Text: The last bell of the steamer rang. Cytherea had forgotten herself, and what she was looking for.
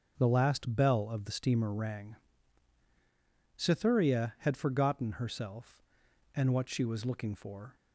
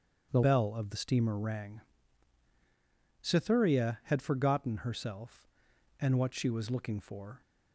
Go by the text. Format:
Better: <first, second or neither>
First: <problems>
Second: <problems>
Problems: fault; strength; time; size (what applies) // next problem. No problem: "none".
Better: first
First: starts louder than the rest; until 1.1 s; 6.5 dB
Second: starts louder than the rest; strong; until 1.3 s; 7.5 dB // skips "last"; at 0.4 s